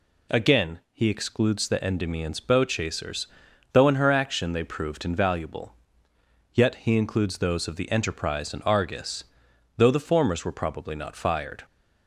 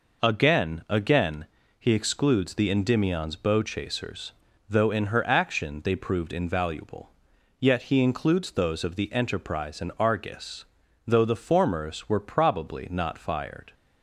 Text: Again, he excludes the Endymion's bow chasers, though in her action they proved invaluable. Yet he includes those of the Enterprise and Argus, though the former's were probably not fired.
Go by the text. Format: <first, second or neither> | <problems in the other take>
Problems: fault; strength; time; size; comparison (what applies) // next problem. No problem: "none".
first | says "Again" twice; at 0.8 s